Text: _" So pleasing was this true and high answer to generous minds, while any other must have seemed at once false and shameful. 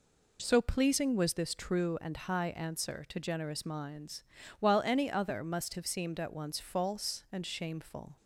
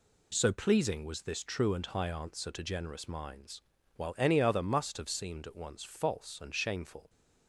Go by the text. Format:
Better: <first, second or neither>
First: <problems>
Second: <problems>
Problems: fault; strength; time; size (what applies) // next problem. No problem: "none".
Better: second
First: changes voice at "So"; from 0.4 s on; 7.7 s long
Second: none